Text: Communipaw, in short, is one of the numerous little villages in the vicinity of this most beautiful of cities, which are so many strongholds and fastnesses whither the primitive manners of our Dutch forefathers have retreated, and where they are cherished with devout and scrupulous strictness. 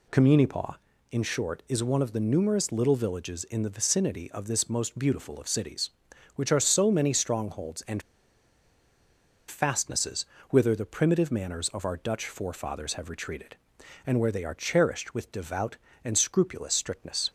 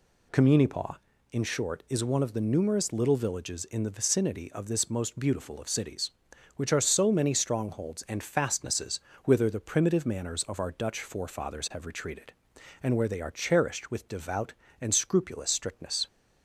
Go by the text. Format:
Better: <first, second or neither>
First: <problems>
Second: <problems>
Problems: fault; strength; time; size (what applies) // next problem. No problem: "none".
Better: second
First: pauses between "and" and "fastnesses"; strong; at 8.0 s; 1.4 s long // pauses between "fastnesses" and "whither"; slight; at 10.2 s; 0.26 s long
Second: pauses between "fastnesses" and "whither"; slight; at 8.9 s; 0.26 s long